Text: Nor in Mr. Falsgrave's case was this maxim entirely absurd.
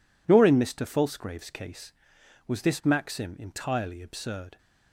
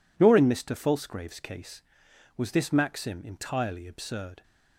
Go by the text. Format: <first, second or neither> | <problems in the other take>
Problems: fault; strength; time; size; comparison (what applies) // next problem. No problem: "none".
neither | none